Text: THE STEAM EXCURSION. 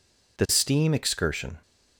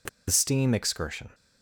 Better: first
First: none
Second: pauses between "THE" and "STEAM"; slight; at 0.0 s; 0.21 s long

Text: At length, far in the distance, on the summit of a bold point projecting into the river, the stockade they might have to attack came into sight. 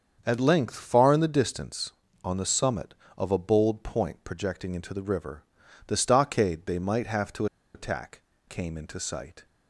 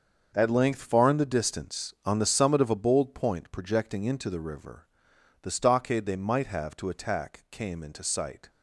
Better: second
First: starts louder than the rest; strong; until 1.2 s; 7.5 dB // pauses between "to" and "attack"; slight; at 7.4 s; 0.29 s long // pauses between "attack" and "came"; slight; at 8.2 s; 0.26 s long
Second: starts louder than the rest; until 1.3 s; 6.5 dB

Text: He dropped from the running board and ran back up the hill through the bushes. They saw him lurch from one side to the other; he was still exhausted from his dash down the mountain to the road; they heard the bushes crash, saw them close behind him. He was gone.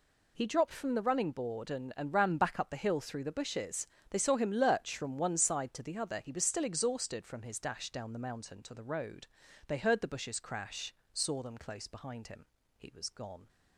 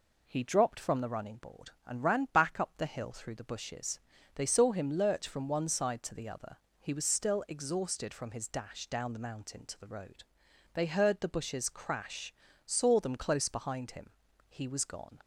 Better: second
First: says "and" twice; at 1.9 s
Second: none

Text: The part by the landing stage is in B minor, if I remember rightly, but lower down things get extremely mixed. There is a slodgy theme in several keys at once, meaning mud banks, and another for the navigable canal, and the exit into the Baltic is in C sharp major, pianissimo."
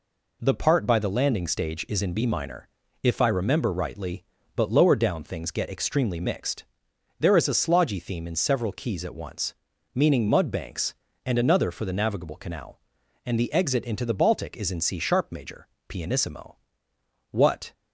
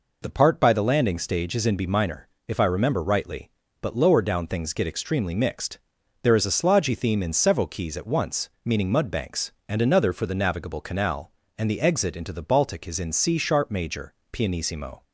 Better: second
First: goes on to say "What"; slight; from 17.2 s on; 0.44 s long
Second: none

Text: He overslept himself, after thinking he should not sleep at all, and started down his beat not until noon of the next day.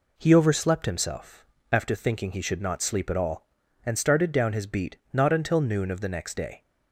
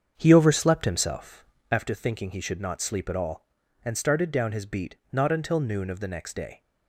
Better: first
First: pauses between "beat" and "not"; slight; at 4.9 s; 0.16 s long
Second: starts louder than the rest; strong; until 1.7 s; 7.5 dB // pauses between "beat" and "not"; slight; at 4.9 s; 0.16 s long

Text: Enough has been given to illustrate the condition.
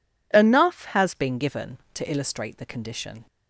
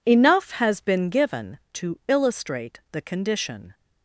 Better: second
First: changes voice at "been"; from 1.1 s on; 2.1 s long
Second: none

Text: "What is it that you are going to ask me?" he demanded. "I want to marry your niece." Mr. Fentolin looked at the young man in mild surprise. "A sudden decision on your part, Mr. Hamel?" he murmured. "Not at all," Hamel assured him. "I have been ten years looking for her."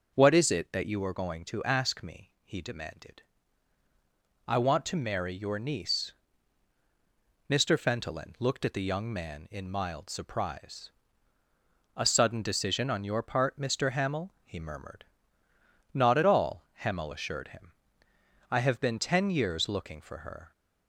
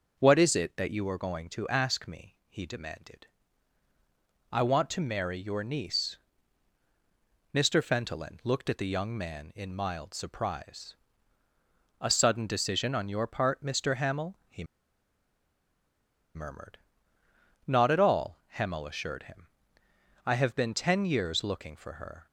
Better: first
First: starts louder than the rest; noticeable; until 1.2 s; 6 dB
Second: starts louder than the rest; until 1.2 s; 6 dB // pauses between "he" and "murmured"; strong; at 14.6 s; 1.7 s long

